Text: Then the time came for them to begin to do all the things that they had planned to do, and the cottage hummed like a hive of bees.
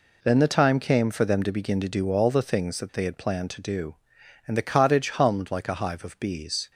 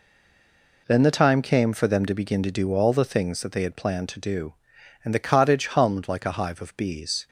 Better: first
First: none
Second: stays silent before the first word; slight; until 0.8 s; 0.8 s long

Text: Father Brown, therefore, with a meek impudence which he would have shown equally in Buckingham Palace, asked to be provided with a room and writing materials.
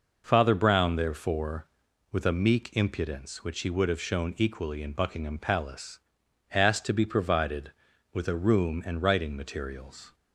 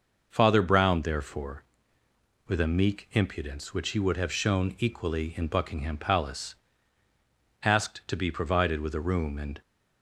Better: first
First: none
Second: stops before "writing materials"; at 9.6 s

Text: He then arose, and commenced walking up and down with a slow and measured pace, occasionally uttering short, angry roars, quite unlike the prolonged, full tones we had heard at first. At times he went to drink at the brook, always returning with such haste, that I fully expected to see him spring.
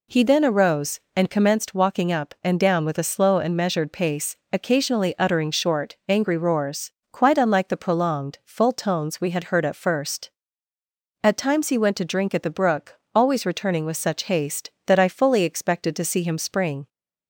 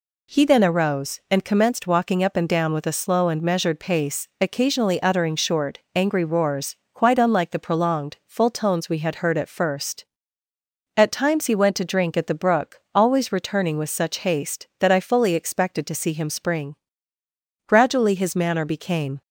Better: first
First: none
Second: goes on to say "Gradually his manner became"; from 17.6 s on; 1.5 s long

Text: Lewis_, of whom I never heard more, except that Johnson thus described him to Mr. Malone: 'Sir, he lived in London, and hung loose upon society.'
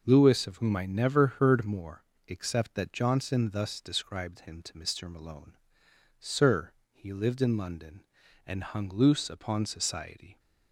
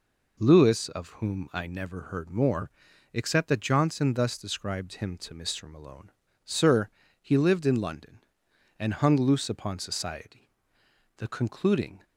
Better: first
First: none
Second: goes on to say "The concluding"; noticeable; from 11.1 s on; 0.88 s long

